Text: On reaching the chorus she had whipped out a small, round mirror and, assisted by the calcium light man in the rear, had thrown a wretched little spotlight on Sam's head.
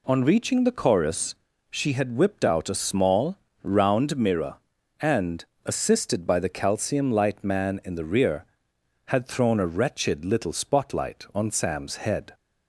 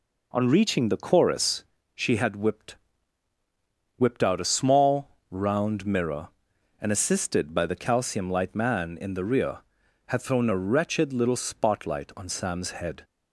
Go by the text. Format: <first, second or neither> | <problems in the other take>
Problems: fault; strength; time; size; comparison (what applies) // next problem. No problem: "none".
first | pauses between "chorus" and "she"; slight; at 1.6 s; 0.30 s long; slight in the first // says "whipped" twice; at 3.9 s